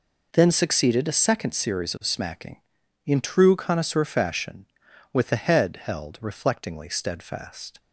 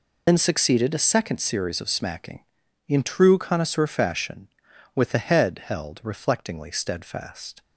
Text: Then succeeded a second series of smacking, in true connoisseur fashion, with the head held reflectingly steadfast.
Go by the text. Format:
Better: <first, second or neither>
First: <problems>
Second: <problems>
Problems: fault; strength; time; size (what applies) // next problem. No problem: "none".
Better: first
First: none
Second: loses the start of "Then"; at 0.2 s; 85 ms